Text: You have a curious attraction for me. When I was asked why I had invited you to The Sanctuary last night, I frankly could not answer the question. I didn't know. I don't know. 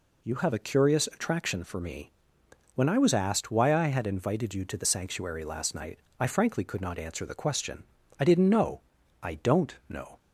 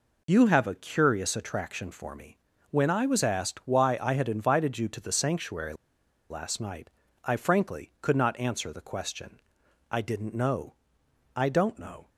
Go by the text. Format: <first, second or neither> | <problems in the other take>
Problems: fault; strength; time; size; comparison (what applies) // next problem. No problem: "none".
first | pauses between "Sanctuary" and "last"; noticeable; at 5.7 s; 0.56 s long